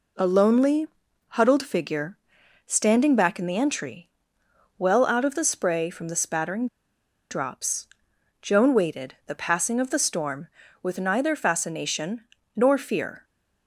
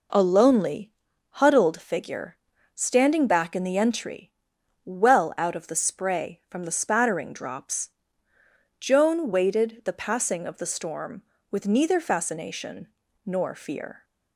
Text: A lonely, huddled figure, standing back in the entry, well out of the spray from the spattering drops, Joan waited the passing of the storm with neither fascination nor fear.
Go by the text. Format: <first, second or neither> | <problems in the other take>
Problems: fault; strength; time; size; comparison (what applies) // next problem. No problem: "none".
second | pauses between "spattering" and "drops"; noticeable; at 6.6 s; 0.64 s long // pauses between "fascination" and "nor"; slight; at 12.2 s; 0.34 s long; also in the second